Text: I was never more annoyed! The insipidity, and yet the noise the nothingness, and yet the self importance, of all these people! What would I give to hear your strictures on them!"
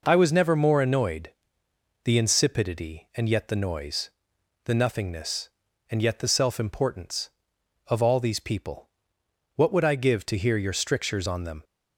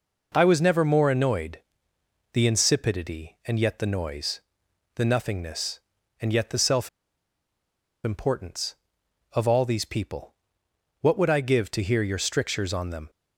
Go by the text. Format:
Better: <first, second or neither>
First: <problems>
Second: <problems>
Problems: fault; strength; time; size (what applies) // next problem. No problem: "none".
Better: first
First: pauses between "noise" and "the"; noticeable; at 4.1 s; 0.54 s long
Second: pauses between "noise" and "the"; noticeable; at 4.4 s; 0.54 s long // pauses between "self" and "importance"; at 6.8 s; 1.1 s long